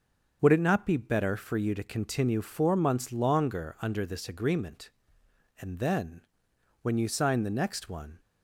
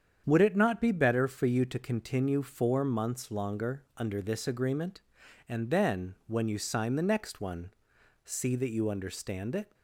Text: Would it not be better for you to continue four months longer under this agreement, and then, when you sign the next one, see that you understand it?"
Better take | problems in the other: second | starts louder than the rest; until 1.4 s; 6.5 dB; strong in the second // stops before "see that you understand it"; at 8.1 s

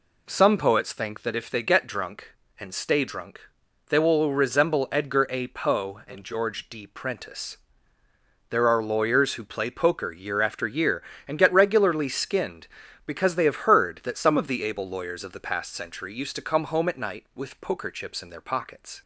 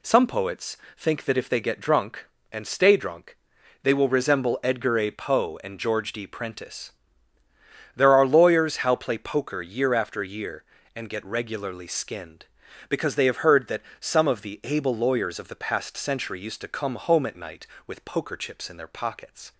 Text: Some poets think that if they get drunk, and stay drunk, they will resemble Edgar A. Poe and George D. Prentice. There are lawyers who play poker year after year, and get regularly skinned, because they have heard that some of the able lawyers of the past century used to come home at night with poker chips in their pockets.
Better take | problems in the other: first | pauses between "poets" and "think"; slight; at 0.7 s; 0.20 s long // says "how" for "who"; at 8.7 s // pauses between "that" and "some"; slight; at 13.8 s; 0.16 s long

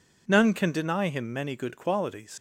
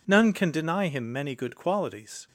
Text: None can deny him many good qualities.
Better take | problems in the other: second | leaves "qualities" unfinished; at 2.3 s; 95 ms

